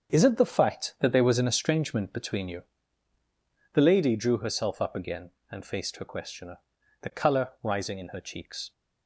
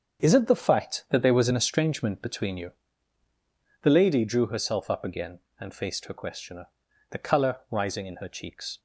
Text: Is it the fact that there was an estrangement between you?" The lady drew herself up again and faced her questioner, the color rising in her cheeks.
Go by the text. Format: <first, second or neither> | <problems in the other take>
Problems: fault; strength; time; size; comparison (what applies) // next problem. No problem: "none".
neither | starts louder than the rest; the same in both